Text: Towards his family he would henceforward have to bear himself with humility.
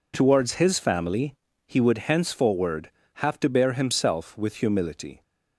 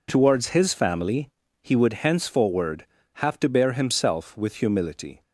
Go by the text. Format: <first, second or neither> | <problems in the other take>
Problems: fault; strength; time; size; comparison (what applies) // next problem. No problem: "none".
neither | pauses between "family" and "he"; slight; the same in both